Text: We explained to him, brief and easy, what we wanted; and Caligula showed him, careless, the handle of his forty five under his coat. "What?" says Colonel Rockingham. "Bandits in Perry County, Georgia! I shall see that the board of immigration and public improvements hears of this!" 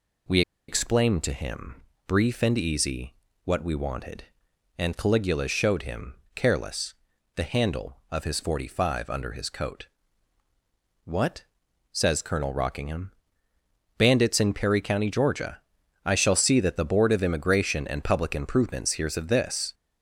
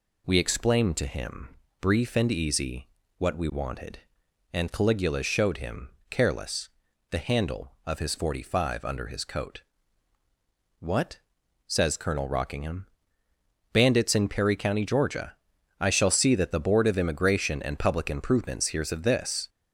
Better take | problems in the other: second | pauses between "We" and "explained"; slight; at 0.4 s; 0.27 s long

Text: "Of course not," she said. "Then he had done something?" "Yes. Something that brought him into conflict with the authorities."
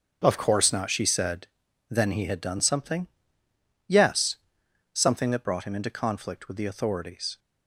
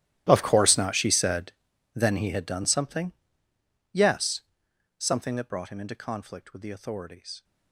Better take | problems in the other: first | gets quieter; strong; throughout; 20 dB // starts louder than the rest; strong; until 1.2 s; 13 dB; also in the first

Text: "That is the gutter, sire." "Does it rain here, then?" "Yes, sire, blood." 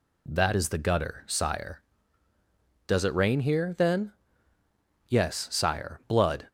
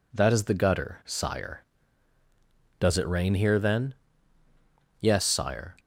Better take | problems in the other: first | stops before "blood"; at 5.7 s

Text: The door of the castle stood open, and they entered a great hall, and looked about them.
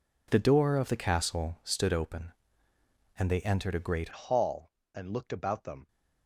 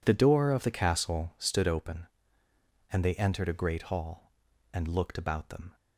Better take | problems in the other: second | changes voice at "hall"; from 4.1 s on; 1.7 s long

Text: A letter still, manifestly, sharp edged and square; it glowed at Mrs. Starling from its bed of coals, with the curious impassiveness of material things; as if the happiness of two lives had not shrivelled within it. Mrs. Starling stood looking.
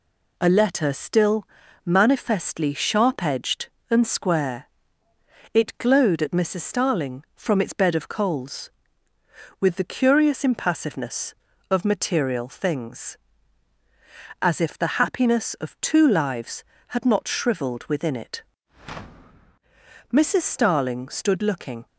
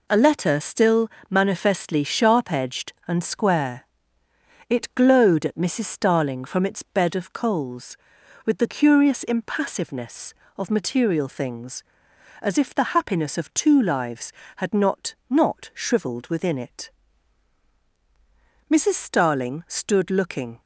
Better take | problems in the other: first | says "not" twice; at 15.2 s

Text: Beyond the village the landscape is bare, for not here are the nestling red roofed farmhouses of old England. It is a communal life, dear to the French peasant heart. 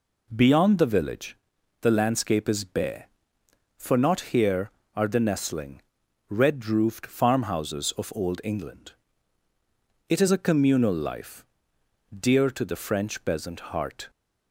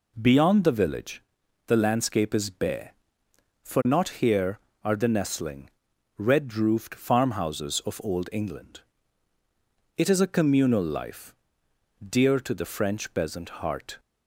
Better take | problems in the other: neither | pauses between "village" and "the"; the same in both // pauses between "nestling" and "red"; noticeable; the same in both

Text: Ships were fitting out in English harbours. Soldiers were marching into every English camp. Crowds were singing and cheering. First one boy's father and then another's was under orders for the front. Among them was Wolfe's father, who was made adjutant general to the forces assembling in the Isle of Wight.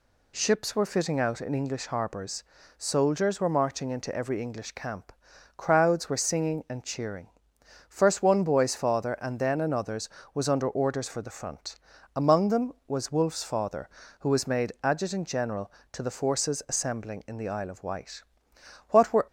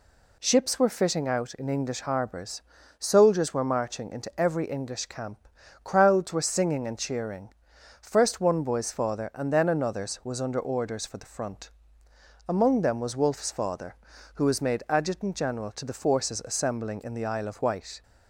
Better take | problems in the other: second | goes on to say "What were"; slight; from 18.8 s on; 0.38 s long

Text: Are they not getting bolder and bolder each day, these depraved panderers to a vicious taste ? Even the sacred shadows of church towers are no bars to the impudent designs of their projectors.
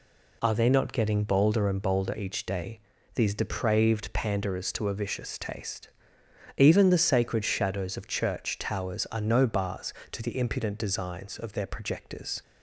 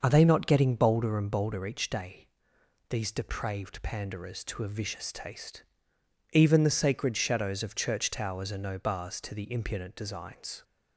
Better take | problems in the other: first | starts louder than the rest; until 1.0 s; 6 dB // stops before "of their projectors"; at 10.6 s

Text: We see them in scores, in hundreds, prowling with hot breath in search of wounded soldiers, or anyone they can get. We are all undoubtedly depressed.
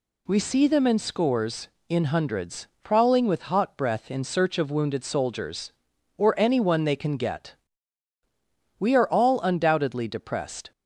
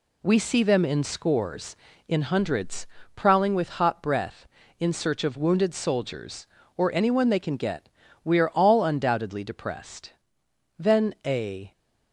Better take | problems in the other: first | goes on to say "Then a"; noticeable; from 10.7 s on; 0.94 s long

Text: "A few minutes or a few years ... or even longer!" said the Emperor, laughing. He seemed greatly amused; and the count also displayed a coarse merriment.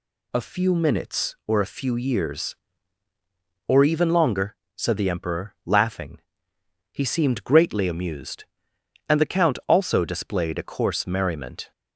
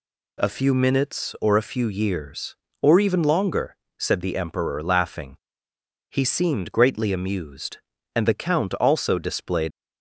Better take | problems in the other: first | stops before "a coarse merriment"; at 9.7 s

